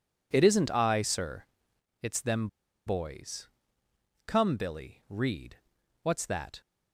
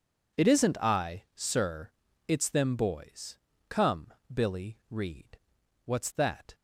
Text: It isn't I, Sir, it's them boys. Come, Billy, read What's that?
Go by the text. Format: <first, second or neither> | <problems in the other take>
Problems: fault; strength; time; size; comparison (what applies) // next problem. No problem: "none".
second | pauses between "them" and "boys"; at 2.4 s; 0.38 s long // pauses between "read" and "What's"; noticeable; at 5.5 s; 0.46 s long; noticeable in the second